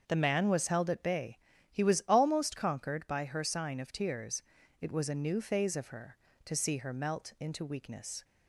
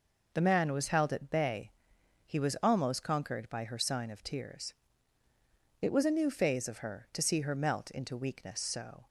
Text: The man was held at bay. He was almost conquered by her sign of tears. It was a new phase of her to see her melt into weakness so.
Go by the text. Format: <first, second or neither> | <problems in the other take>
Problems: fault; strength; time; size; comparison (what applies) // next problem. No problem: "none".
second | starts louder than the rest; until 1.0 s; 6.5 dB // stops before "so"; at 8.2 s